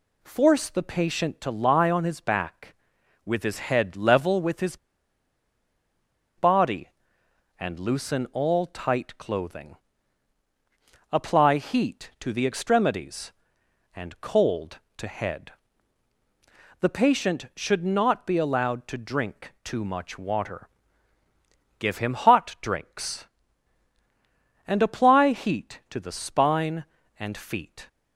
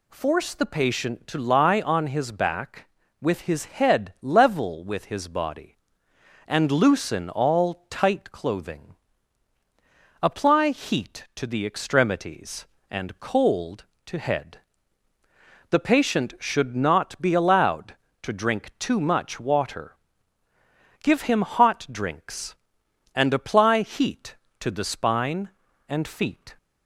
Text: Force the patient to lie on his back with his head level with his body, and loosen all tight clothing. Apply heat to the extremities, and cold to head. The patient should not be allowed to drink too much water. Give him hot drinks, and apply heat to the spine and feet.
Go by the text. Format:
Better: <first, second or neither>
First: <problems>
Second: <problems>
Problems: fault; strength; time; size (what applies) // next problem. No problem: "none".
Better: second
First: pauses between "his" and "body"; strong; at 4.7 s; 1.6 s long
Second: none